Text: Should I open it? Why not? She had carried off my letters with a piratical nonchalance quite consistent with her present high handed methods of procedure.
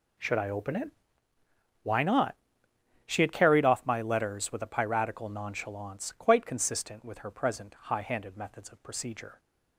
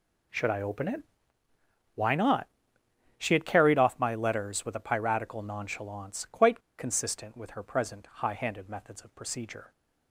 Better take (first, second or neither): first